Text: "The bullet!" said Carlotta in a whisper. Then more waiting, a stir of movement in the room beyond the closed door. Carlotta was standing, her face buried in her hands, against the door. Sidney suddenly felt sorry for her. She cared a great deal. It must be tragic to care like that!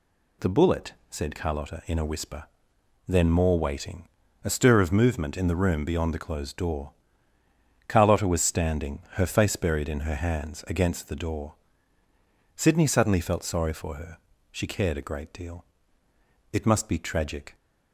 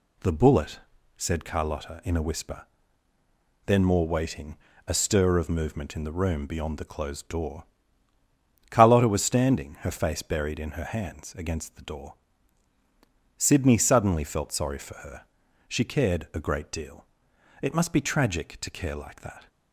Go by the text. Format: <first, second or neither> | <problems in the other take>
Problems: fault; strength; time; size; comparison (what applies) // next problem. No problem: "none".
second | stops before "to care like that"; at 17.5 s